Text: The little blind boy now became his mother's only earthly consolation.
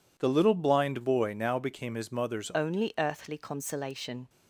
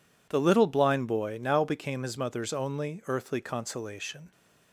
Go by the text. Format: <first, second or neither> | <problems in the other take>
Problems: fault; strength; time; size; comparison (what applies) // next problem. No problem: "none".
second | changes voice at "only"; from 2.5 s on; 1.7 s long